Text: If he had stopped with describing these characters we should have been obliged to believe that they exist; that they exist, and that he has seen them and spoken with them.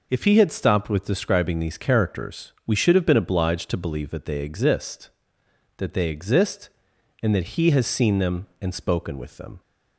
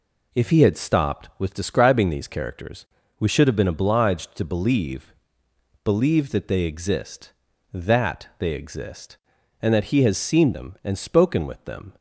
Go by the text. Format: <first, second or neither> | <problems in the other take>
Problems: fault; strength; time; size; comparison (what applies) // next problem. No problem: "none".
first | pauses between "characters" and "we"; slight; at 2.8 s; 0.32 s long // says "believe" twice; at 5.8 s